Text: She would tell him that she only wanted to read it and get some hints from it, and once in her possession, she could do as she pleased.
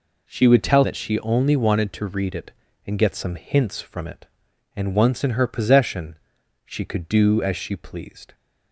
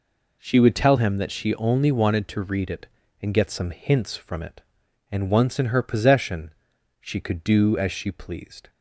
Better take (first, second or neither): second